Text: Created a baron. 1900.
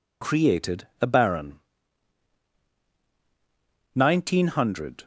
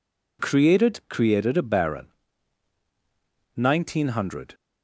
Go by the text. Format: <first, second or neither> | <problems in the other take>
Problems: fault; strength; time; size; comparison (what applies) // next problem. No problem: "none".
first | says "Created" twice; at 1.1 s